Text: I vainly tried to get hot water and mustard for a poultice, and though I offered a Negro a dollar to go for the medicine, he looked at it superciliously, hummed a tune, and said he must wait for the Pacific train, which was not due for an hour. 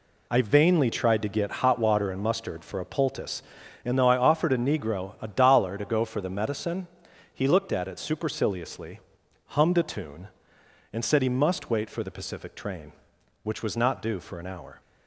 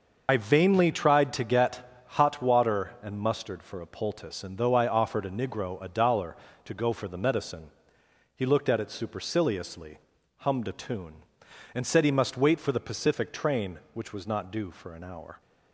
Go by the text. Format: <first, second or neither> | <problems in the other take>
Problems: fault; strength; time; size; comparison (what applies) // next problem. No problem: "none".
first | loses the start of "I"; at 0.2 s; 65 ms // starts louder than the rest; until 1.2 s; 6.5 dB